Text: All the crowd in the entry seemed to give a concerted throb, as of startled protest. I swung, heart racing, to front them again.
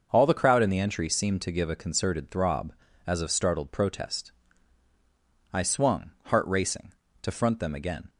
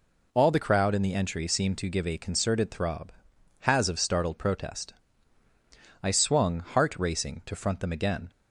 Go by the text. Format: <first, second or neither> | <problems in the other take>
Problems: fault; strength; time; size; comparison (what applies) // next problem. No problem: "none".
first | says "has" for "as"; at 3.6 s